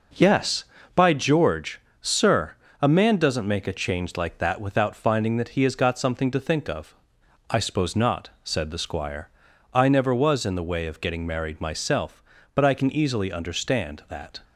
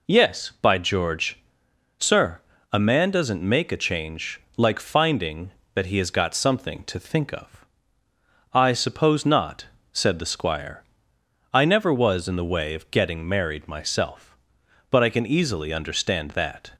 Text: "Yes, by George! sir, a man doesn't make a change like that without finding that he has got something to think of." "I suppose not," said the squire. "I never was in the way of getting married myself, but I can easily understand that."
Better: first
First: none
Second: pauses between "change" and "like"; slight; at 4.4 s; 0.16 s long // skips "that without"; at 4.7 s

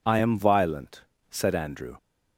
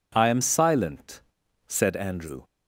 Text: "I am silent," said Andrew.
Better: second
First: says "violent" for "silent"; at 0.3 s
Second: none

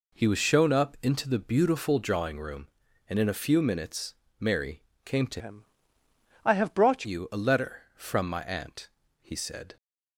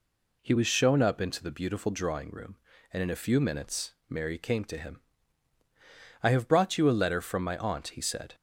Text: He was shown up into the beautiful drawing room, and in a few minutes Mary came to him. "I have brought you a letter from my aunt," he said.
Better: second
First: pauses between "minutes" and "Mary"; slight; at 4.1 s; 0.24 s long // pauses between "Mary" and "came"; slight; at 4.8 s; 0.22 s long // changes voice from "him" to "brought"; from 5.3 to 7.0 s; 1.7 s long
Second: pauses between "minutes" and "Mary"; slight; at 3.9 s; 0.16 s long

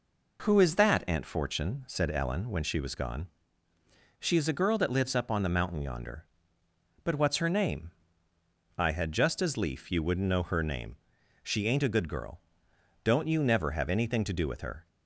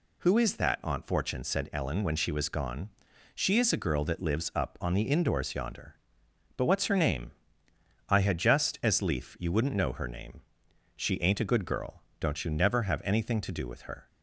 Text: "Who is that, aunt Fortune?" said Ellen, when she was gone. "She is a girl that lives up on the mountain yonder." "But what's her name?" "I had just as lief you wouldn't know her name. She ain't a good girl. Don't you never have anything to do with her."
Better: first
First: none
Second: says "indoors" for "mountain"; at 5.0 s

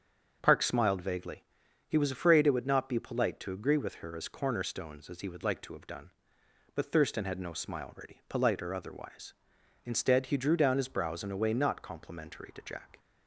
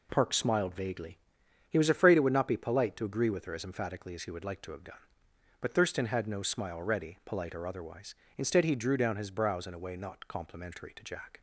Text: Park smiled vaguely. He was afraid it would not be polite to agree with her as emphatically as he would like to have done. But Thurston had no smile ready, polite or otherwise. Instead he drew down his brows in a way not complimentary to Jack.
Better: second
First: starts louder than the rest; until 1.4 s; 7 dB // says "cornerstones" for "emphatically"; at 4.2 s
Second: none

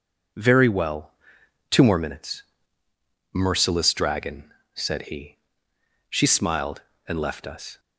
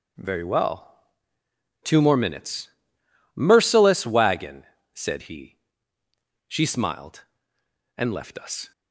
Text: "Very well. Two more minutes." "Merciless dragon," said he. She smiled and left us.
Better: first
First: none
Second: says "wagon" for "dragon"; at 4.0 s

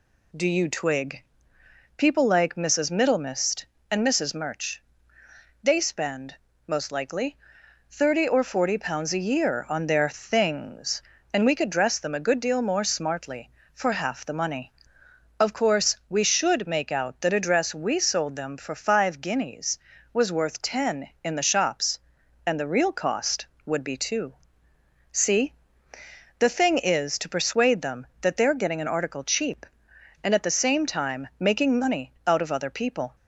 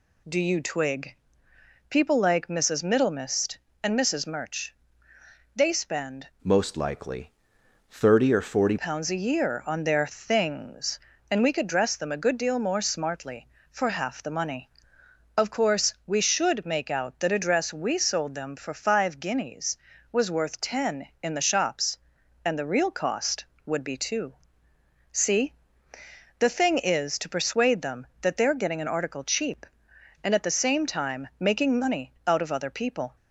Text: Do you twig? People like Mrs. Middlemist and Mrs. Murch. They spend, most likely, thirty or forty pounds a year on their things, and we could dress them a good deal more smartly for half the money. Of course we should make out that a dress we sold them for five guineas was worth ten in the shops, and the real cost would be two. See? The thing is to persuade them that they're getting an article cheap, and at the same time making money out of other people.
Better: first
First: none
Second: changes voice from "most" to "forty"; from 6.4 to 8.7 s; 2.3 s long

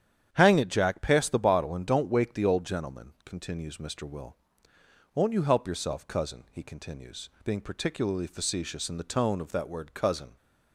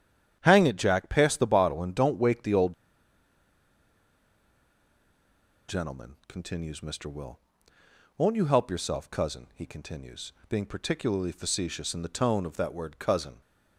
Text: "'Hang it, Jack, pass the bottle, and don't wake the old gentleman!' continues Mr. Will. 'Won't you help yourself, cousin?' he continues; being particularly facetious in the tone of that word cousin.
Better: first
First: starts louder than the rest; strong; until 1.3 s; 9 dB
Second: starts louder than the rest; strong; until 1.4 s; 9 dB // pauses between "old" and "gentleman"; strong; at 2.7 s; 2.9 s long

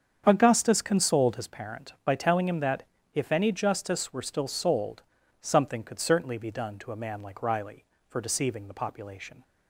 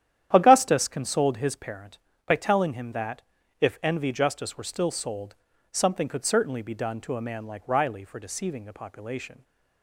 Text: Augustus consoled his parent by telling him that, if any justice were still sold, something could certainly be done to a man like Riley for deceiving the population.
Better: first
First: starts louder than the rest; strong; until 1.2 s; 7.5 dB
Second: starts louder than the rest; strong; until 1.3 s; 10.5 dB // says "envy" for "any"; at 3.8 s

